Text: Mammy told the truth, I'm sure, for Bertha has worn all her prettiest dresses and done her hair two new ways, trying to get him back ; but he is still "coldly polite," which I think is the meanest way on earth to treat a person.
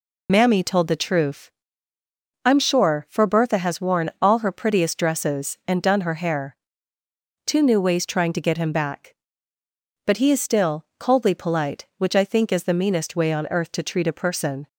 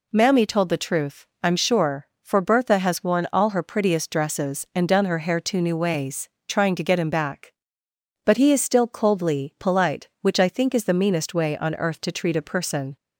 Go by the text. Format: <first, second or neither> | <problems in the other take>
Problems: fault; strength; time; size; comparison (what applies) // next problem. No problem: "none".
second | loses the start of "Mammy"; at 0.2 s; 35 ms // pauses between "hair" and "two"; noticeable; at 6.5 s; 0.90 s long